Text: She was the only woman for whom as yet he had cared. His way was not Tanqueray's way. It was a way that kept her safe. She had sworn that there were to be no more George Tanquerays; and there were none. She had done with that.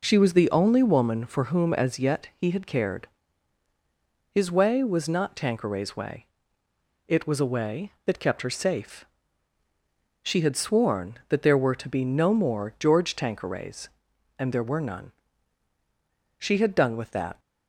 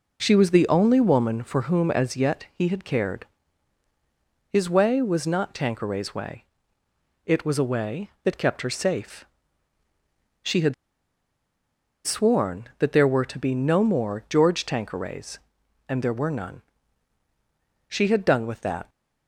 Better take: first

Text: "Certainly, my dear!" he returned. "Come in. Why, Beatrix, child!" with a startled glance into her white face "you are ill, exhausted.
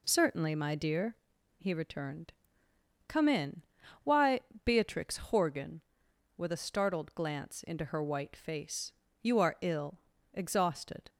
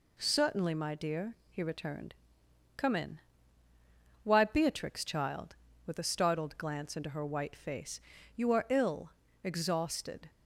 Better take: second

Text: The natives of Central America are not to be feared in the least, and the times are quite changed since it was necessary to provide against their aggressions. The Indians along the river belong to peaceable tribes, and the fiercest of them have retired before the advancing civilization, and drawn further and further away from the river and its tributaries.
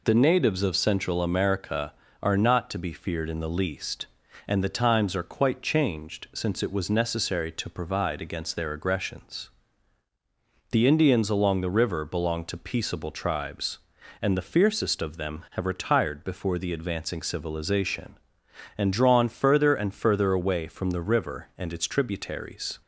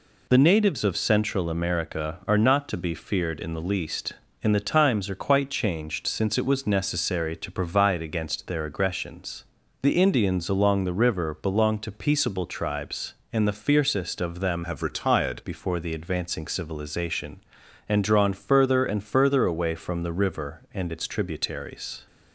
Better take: first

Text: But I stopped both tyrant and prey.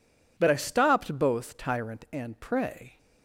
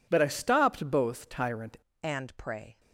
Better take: first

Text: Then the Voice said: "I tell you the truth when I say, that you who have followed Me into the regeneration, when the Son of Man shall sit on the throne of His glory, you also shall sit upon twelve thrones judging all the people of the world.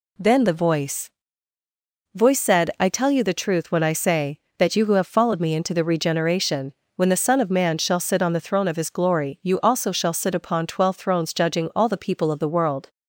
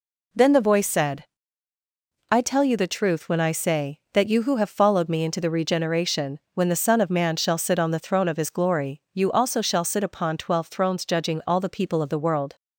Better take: second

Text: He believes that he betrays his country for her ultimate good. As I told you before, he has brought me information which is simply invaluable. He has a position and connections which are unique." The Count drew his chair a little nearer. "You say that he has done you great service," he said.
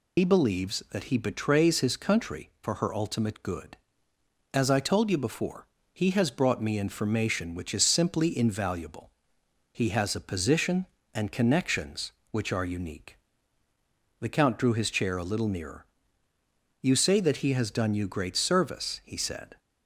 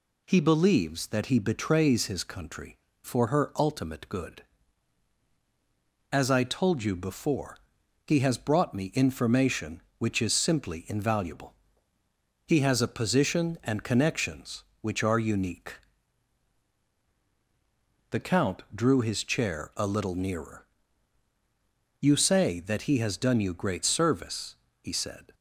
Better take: second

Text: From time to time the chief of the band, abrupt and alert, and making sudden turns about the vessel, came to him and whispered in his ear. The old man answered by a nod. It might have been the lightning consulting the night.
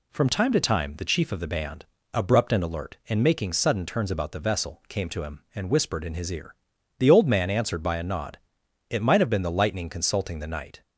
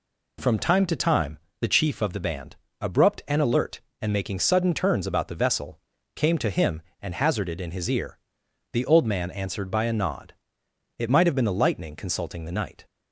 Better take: first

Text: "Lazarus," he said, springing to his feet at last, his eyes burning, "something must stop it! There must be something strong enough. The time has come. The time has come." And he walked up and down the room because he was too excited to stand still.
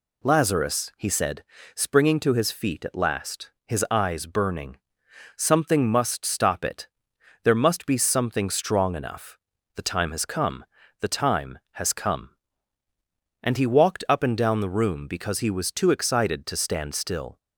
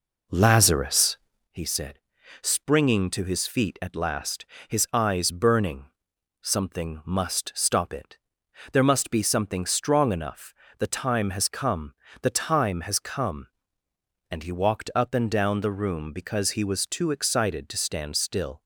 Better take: first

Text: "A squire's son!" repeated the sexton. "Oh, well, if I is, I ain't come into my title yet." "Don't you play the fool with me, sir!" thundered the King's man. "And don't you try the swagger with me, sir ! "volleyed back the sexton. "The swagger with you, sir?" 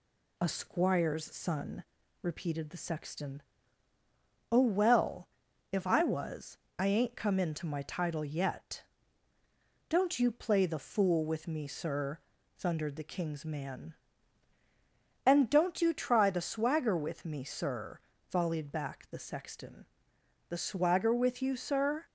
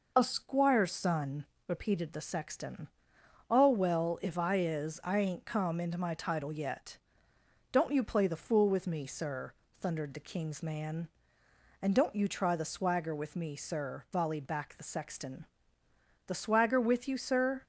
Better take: second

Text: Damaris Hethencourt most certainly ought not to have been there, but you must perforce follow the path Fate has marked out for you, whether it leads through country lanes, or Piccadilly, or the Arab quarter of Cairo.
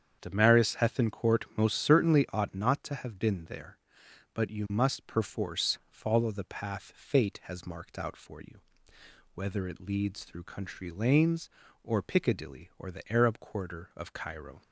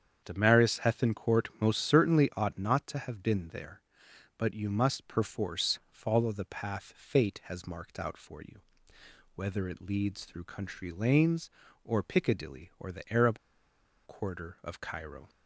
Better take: first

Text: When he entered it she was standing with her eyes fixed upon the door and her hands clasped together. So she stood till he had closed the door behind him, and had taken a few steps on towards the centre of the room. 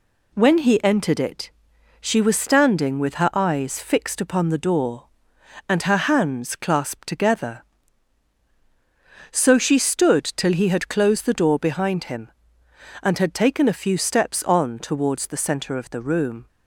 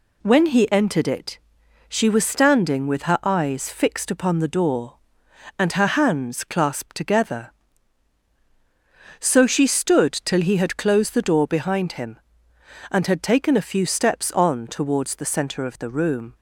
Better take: neither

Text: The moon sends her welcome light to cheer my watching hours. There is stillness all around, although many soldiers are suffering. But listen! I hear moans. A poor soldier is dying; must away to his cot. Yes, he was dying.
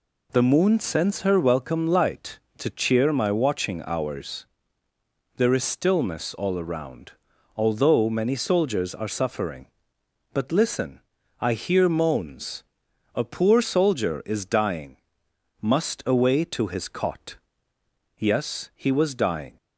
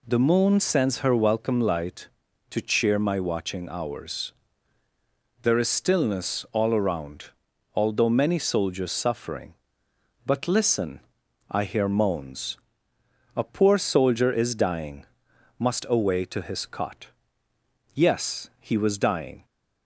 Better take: first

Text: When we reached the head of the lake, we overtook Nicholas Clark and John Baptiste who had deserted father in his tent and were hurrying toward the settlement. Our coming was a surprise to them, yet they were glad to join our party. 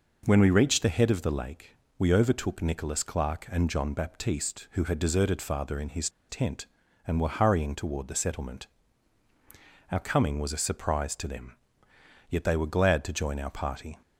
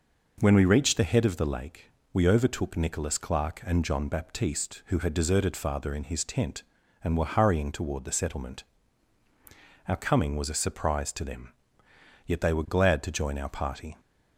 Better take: second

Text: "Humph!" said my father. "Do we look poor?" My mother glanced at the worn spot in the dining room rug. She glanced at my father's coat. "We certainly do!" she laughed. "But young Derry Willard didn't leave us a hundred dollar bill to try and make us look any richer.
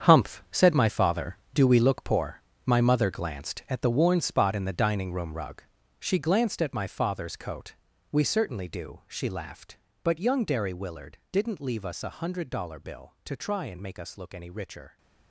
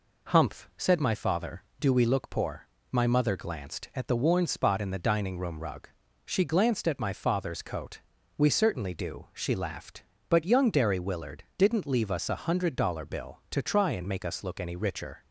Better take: second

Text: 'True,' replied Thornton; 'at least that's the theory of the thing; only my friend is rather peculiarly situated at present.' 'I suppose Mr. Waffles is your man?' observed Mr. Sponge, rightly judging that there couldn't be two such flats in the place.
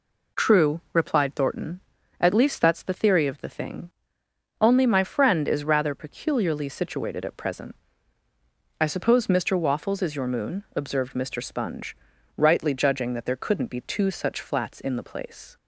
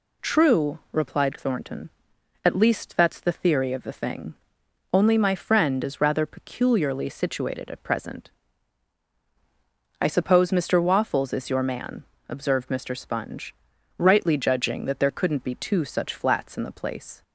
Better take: second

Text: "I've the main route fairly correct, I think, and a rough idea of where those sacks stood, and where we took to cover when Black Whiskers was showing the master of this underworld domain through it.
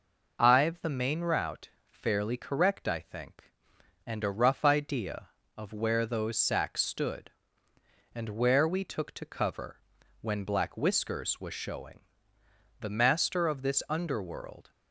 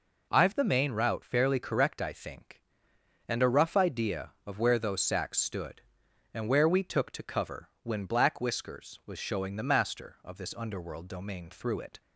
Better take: second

